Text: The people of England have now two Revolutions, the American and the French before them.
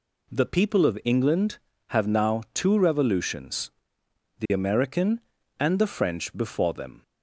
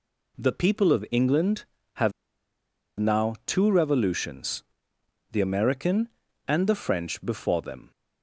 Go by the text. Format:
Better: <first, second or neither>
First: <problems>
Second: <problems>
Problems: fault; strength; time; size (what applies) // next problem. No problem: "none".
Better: first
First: none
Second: pauses between "have" and "now"; noticeable; at 2.1 s; 0.88 s long